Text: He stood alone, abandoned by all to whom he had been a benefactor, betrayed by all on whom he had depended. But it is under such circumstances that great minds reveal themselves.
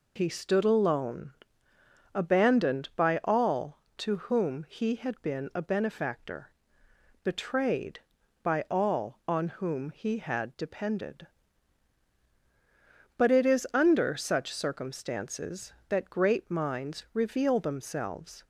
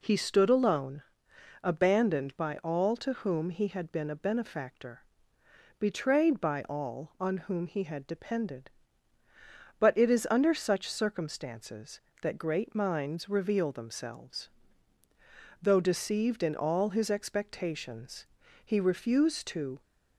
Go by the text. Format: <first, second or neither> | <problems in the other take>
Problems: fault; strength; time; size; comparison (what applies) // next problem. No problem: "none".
first | goes on to say "Though deceived in all his expectations he refused to"; strong; from 15.6 s on; 4.2 s long